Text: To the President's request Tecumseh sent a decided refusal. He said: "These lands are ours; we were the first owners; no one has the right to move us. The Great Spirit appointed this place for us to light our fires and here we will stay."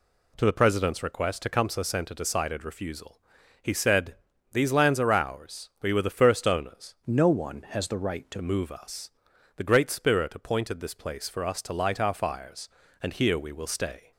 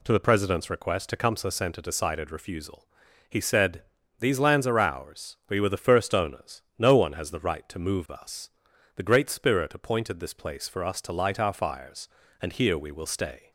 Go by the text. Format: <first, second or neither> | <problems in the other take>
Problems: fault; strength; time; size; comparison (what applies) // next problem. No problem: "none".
second | changes voice from "no" to "to"; from 7.0 to 8.3 s; 1.3 s long